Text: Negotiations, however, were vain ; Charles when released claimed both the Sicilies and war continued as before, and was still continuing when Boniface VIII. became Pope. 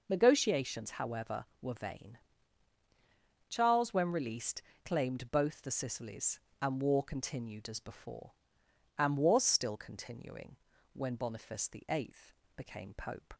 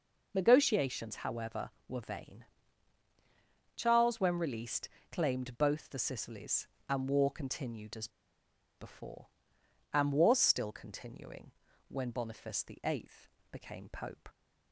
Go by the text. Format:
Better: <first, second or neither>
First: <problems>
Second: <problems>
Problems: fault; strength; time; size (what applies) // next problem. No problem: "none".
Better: first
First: pauses between "released" and "claimed"; slight; at 4.6 s; 0.22 s long // pauses between "continuing" and "when"; at 10.5 s; 0.38 s long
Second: pauses between "released" and "claimed"; slight; at 4.8 s; 0.22 s long // pauses between "as" and "before"; noticeable; at 8.0 s; 0.70 s long // pauses between "continuing" and "when"; at 11.5 s; 0.38 s long